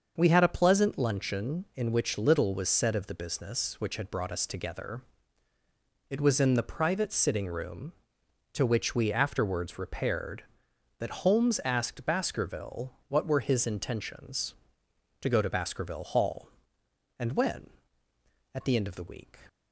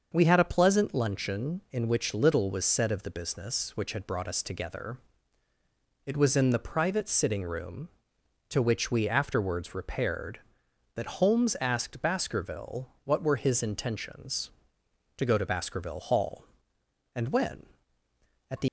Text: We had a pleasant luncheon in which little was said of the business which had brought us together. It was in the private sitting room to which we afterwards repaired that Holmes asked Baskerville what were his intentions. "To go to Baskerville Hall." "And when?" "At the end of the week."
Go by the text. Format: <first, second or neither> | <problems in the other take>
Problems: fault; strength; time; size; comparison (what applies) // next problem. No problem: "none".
first | starts louder than the rest; until 1.1 s; 6.5 dB; also in the first // pauses between "Baskerville" and "what"; slight; at 12.8 s; 0.16 s long; slight in the first // stops before "end of the week"; at 18.6 s